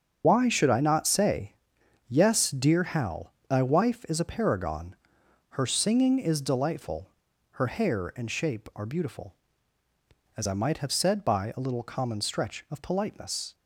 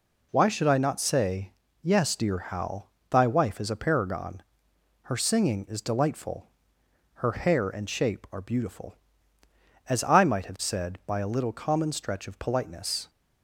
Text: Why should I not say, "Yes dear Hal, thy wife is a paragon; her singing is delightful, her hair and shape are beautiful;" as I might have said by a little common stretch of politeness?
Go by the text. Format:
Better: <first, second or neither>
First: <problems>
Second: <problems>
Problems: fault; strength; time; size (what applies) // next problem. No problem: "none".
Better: second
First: loses the start of "Why"; at 0.2 s; 30 ms // starts louder than the rest; until 1.2 s; 7 dB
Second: none